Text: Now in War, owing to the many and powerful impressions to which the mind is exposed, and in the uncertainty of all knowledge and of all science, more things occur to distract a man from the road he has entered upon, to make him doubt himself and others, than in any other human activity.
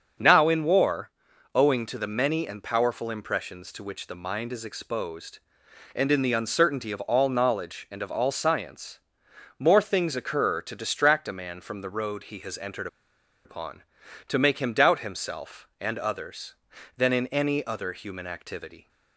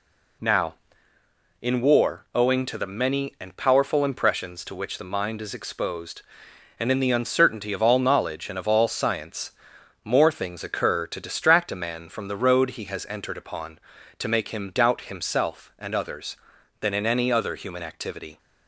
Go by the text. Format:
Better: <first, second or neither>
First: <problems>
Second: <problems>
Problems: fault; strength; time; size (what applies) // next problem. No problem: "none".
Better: second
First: starts louder than the rest; until 1.6 s; 6.5 dB // pauses between "entered" and "upon"; noticeable; at 12.8 s; 0.58 s long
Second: none